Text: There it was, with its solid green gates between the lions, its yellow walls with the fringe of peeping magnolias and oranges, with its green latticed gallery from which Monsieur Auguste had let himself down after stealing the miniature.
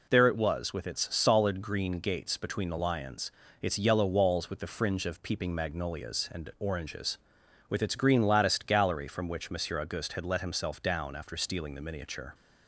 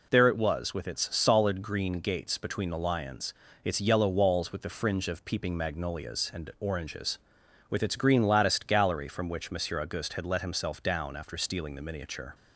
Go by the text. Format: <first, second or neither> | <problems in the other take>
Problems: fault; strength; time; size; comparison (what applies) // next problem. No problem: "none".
neither | none